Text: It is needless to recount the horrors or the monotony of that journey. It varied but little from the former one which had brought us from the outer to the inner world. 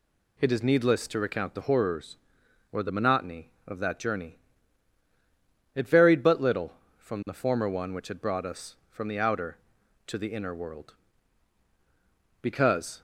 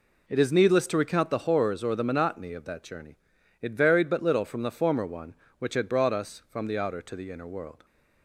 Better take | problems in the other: second | goes on to say "Because"; from 12.4 s on; 0.60 s long

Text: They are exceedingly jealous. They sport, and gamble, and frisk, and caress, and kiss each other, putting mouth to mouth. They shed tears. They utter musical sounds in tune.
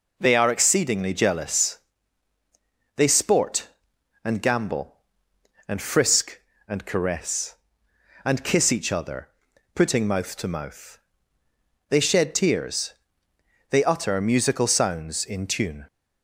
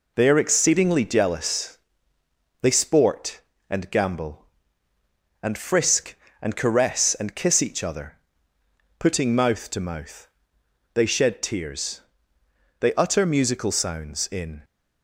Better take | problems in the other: first | stops before "tune"; at 14.6 s

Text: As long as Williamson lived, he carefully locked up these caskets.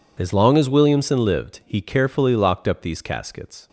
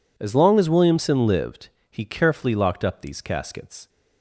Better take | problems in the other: neither | none

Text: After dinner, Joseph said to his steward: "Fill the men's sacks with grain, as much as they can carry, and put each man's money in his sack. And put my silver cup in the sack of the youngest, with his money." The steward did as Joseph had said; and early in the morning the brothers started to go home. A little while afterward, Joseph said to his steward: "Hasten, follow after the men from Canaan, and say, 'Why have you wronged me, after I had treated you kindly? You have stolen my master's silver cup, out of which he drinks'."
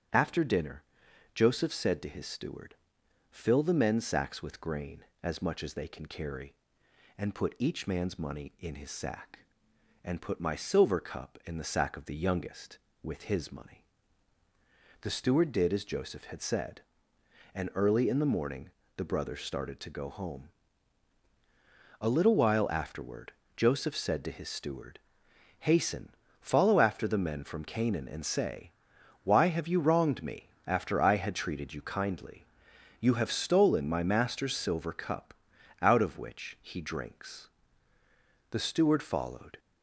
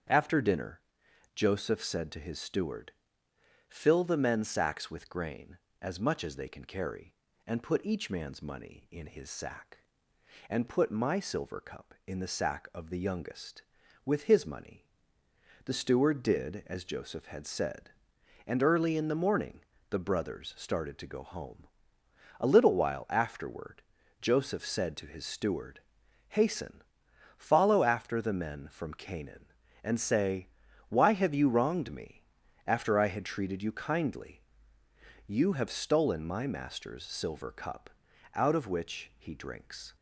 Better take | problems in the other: second | starts louder than the rest; strong; until 1.6 s; 9.5 dB; strong in the second // pauses between "morning" and "the"; slight; at 18.6 s; 0.26 s long; slight in the second // goes on to say "The steward followed"; noticeable; from 38.5 s on; 1.0 s long

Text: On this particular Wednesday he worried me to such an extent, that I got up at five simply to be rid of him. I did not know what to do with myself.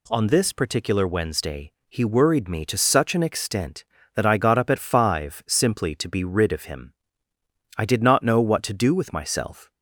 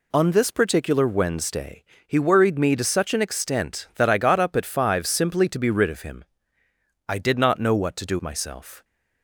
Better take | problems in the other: first | pauses between "Wednesday" and "he"; slight; at 1.8 s; 0.20 s long; slight in the first // skips "with"; at 8.1 s

